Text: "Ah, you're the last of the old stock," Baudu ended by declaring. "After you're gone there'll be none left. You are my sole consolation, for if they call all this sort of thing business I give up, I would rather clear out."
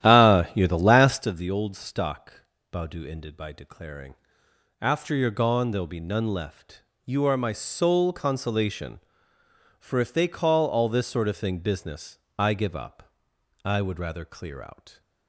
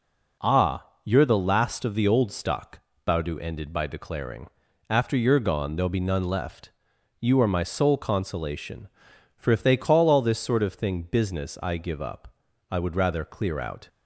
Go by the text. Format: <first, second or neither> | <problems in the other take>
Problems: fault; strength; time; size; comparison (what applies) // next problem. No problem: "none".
second | starts louder than the rest; strong; until 1.4 s; 12 dB // pauses between "business" and "I"; slight; at 12.1 s; 0.20 s long